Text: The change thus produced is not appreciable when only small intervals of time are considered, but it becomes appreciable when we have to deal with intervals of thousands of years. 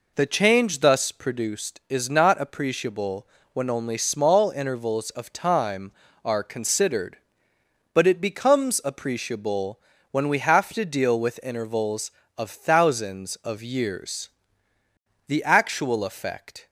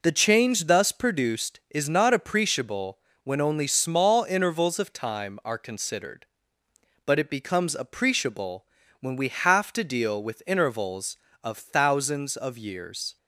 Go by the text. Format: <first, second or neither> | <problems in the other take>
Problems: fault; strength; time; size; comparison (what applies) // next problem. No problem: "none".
second | pauses between "appreciable" and "when"; slight; at 3.2 s; 0.26 s long; slight in the second // pauses between "appreciable" and "when"; slight; at 9.8 s; 0.32 s long; slight in the second // goes on to say "The actual effect"; from 15.2 s on; 1.4 s long